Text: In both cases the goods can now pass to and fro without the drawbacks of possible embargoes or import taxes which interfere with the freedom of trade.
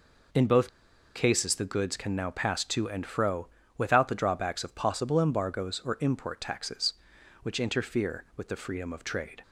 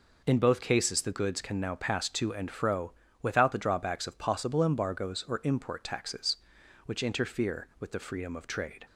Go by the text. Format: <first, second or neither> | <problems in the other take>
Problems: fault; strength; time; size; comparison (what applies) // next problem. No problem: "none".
second | pauses between "both" and "cases"; noticeable; at 0.6 s; 0.46 s long // pauses between "fro" and "without"; slight; at 3.4 s; 0.30 s long; slight in the second